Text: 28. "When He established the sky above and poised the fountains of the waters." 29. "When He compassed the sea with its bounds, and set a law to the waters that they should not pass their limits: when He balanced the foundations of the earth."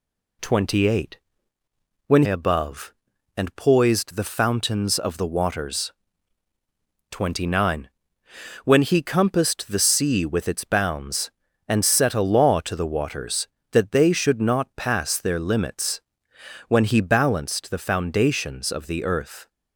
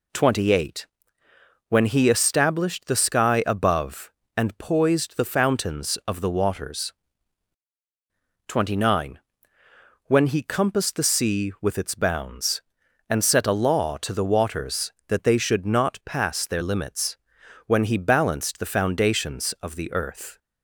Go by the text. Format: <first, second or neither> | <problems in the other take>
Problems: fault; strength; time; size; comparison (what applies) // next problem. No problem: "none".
second | skips "He established the sky"; at 2.2 s